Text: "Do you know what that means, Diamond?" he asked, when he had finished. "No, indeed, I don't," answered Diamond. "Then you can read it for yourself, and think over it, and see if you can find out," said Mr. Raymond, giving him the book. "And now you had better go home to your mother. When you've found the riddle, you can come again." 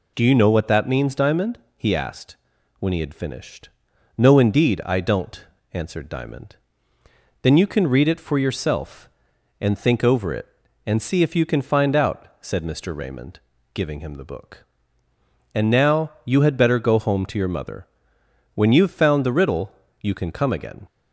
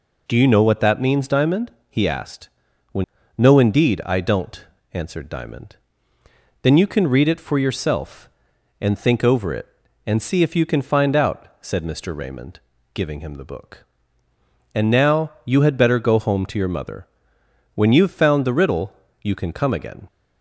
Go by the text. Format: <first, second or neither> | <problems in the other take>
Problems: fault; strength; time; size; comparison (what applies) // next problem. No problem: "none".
first | skips "he had finished"; at 3.2 s